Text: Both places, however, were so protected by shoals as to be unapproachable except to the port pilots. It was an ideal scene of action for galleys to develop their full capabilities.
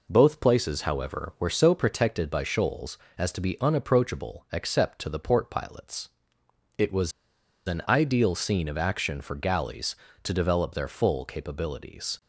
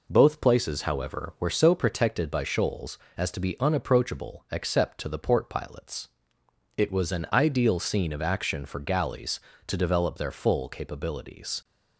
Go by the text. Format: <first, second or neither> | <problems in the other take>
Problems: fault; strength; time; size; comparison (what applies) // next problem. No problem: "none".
second | pauses between "was" and "an"; noticeable; at 7.1 s; 0.55 s long